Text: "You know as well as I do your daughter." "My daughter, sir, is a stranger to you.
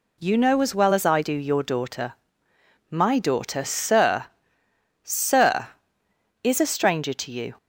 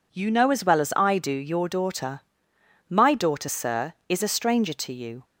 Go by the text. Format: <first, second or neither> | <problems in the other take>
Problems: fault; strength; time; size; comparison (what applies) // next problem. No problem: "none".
second | says "sir" twice; at 5.0 s